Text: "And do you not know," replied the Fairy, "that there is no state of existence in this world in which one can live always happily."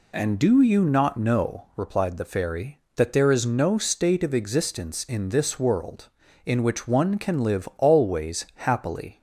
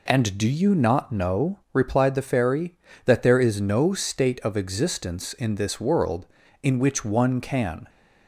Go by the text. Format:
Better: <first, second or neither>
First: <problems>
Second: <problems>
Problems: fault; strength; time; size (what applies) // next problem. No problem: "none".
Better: first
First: none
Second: stops before "live always happily"; at 7.8 s